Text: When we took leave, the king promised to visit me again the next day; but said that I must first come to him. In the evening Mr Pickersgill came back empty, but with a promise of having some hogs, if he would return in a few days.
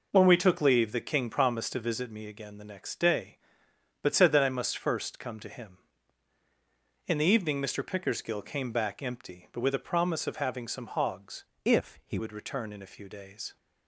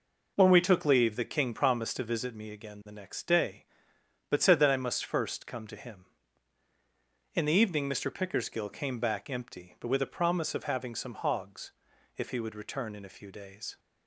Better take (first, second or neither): second